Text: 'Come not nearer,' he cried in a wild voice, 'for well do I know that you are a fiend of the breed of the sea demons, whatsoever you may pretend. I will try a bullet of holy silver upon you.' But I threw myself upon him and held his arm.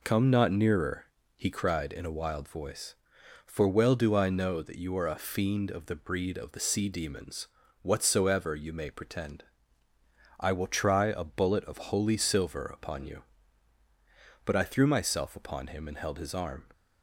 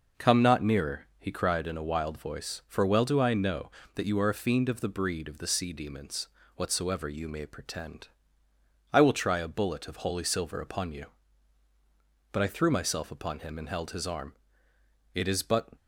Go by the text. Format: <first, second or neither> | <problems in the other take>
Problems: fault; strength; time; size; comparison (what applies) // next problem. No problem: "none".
first | goes on to say "It is but"; from 15.1 s on; 0.56 s long